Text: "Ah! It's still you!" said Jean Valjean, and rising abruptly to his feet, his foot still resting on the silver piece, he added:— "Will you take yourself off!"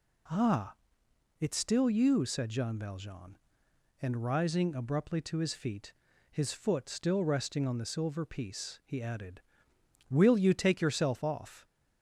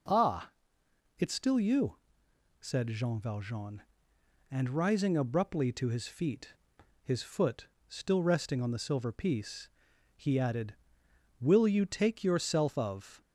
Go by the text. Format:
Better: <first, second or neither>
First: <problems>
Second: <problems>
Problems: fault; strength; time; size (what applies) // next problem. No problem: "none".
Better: first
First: none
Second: pauses between "foot" and "still"; slight; at 7.6 s; 0.22 s long // says "of" for "off"; at 12.7 s